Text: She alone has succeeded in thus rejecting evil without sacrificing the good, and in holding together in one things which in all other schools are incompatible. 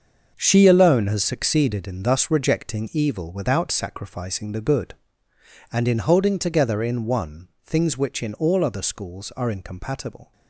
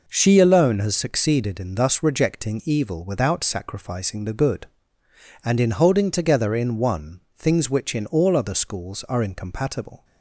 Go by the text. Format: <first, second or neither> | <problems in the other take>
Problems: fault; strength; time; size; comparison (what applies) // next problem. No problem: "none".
second | gets quieter; strong; throughout; 10.5 dB // pauses between "one" and "things"; slight; at 7.4 s; 0.16 s long; slight in the second